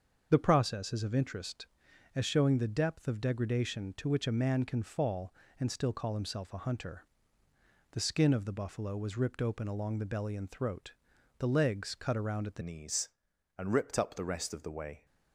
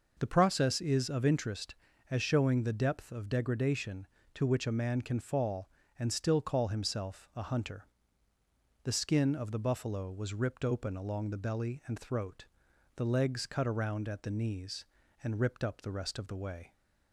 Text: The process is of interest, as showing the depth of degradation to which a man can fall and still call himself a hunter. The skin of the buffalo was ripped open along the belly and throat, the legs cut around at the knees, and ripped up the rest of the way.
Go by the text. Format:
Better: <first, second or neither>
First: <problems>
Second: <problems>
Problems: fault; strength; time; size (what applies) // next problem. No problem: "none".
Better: second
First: starts louder than the rest; until 1.3 s; 7 dB // changes voice at "knees"; from 12.6 s on; 2.4 s long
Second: none